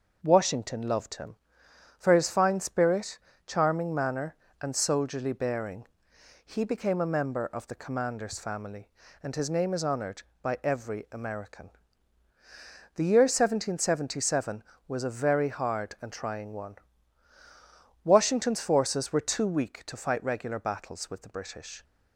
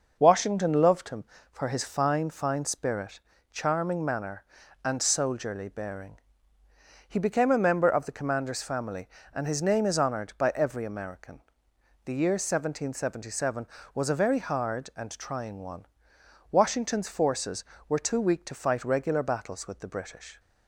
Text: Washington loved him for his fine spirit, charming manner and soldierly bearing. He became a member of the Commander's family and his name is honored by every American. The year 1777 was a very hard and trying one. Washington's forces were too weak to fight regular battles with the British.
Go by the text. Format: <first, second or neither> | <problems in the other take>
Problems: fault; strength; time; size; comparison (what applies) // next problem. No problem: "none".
first | starts louder than the rest; noticeable; until 1.2 s; 6 dB // says "fine" twice; at 2.3 s